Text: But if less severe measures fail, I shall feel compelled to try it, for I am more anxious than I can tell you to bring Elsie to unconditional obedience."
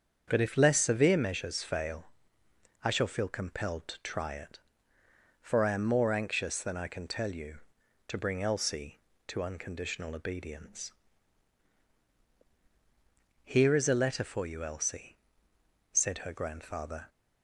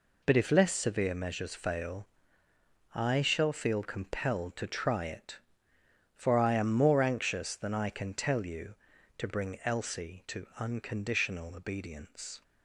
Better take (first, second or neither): second